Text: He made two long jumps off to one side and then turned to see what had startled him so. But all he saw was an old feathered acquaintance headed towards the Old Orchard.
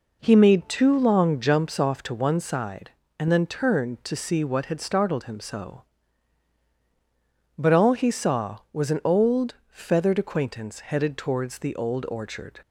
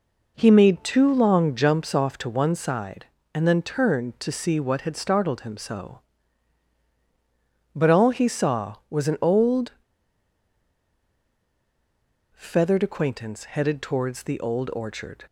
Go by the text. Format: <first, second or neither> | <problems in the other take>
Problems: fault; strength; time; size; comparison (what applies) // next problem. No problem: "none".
first | pauses between "old" and "feathered"; strong; at 9.7 s; 2.6 s long